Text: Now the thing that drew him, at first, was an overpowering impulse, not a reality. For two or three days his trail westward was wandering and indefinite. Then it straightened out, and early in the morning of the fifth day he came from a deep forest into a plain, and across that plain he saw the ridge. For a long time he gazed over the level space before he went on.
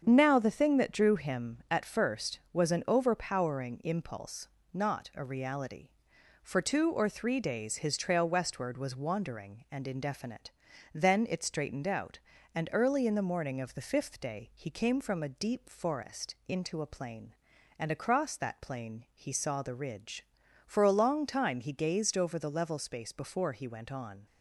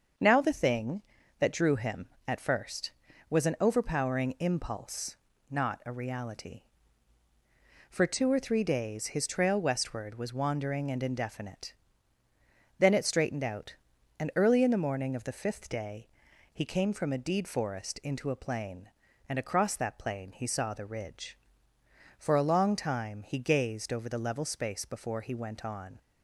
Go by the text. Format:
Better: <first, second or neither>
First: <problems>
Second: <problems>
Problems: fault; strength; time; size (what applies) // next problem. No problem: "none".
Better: first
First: starts louder than the rest; strong; until 1.0 s; 7 dB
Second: starts louder than the rest; until 1.5 s; 6.5 dB // pauses between "day" and "he"; at 16.0 s; 0.42 s long // says "deed" for "deep"; at 17.1 s